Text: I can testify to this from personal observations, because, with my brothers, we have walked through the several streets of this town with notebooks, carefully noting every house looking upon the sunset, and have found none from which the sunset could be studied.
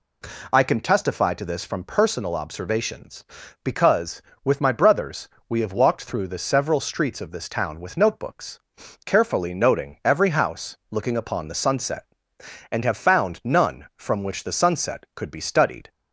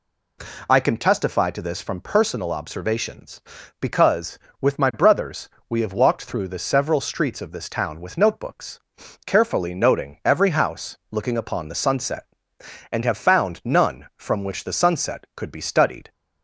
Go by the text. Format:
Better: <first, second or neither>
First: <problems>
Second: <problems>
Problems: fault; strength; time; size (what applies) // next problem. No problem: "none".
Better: neither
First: none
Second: none